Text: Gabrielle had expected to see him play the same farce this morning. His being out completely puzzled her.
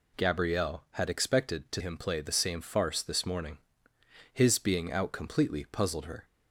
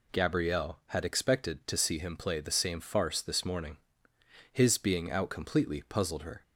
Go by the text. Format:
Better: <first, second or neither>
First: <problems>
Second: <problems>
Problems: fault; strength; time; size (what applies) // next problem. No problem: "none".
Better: second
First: skips "see"; at 1.8 s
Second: none